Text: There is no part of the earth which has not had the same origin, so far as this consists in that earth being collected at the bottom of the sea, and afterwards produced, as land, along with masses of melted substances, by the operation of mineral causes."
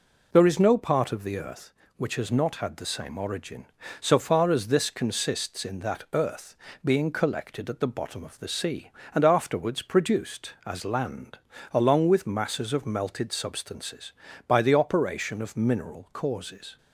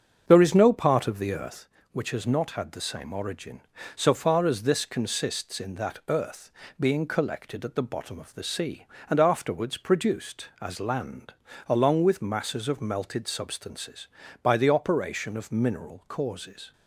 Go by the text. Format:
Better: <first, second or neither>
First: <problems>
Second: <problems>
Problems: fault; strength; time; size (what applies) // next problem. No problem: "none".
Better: first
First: pauses between "earth" and "being"; slight; at 6.5 s; 0.30 s long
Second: starts louder than the rest; until 1.7 s; 7 dB // pauses between "earth" and "being"; slight; at 6.5 s; 0.30 s long